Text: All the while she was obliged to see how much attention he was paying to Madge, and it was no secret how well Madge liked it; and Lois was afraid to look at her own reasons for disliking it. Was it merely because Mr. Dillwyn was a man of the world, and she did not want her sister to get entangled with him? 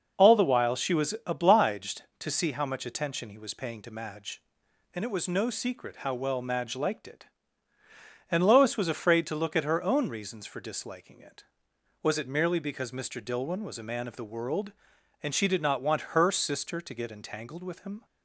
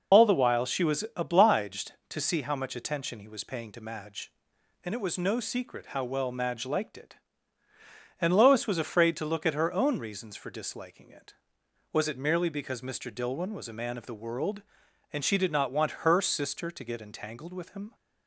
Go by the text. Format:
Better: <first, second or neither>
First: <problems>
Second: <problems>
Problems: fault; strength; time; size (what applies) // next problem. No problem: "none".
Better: first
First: none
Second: loses the start of "All"; at 0.1 s; 50 ms